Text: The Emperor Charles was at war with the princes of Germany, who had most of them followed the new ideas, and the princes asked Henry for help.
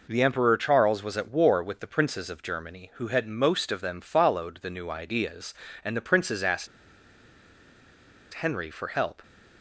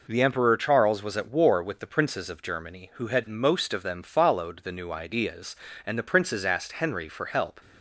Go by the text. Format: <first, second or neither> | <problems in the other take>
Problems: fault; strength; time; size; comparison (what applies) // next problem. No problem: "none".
second | pauses between "asked" and "Henry"; strong; at 6.6 s; 1.6 s long